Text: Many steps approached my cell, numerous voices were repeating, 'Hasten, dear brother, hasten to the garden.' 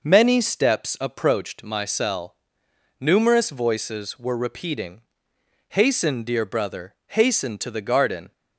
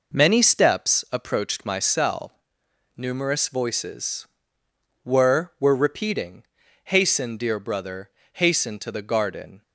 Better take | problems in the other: first | says "were" twice; at 5.5 s

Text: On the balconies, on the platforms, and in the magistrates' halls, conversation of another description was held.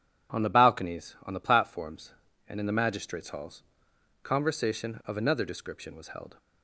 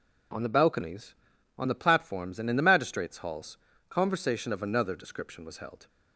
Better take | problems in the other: neither | none

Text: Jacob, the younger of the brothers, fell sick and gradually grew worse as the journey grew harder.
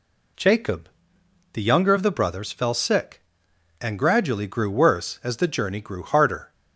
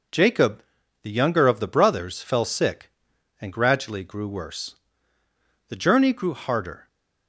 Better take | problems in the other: first | skips "as"; at 5.2 s

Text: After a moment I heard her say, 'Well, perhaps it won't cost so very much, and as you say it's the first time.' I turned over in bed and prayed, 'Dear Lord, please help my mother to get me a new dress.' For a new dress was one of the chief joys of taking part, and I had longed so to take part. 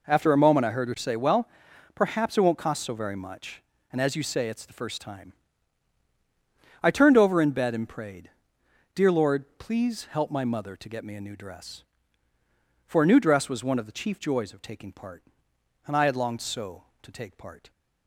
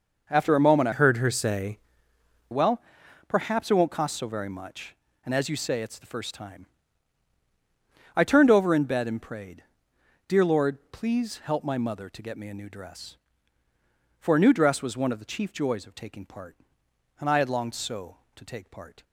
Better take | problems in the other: first | changes voice from "heard" to "say"; from 0.9 to 1.7 s; 0.8 s long

